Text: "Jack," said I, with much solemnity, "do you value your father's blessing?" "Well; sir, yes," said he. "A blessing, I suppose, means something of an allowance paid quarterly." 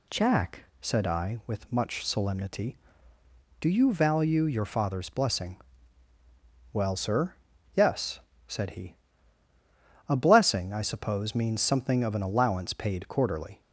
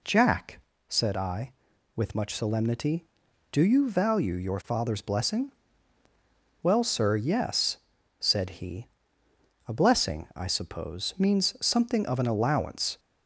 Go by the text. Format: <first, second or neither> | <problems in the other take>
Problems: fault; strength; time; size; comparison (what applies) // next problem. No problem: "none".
first | stops before "paid quarterly"; at 12.9 s